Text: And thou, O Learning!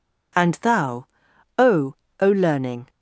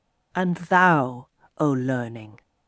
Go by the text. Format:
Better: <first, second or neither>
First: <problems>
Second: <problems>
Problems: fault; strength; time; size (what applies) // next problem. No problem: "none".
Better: second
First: says "O" twice; at 2.1 s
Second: none